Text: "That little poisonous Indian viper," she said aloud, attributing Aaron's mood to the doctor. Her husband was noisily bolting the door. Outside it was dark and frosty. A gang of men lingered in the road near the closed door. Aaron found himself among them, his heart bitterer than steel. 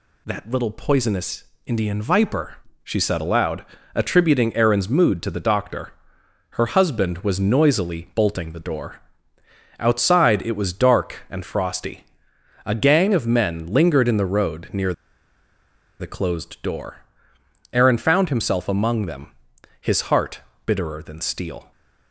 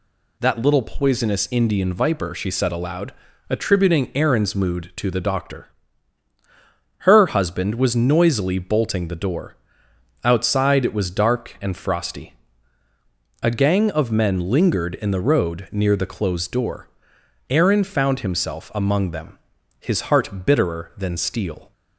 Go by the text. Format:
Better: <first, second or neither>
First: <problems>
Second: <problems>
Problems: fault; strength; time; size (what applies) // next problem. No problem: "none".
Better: second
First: pauses between "poisonous" and "Indian"; slight; at 1.4 s; 0.20 s long // pauses between "near" and "the"; at 14.9 s; 1.0 s long // pauses between "heart" and "bitterer"; slight; at 20.4 s; 0.24 s long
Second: none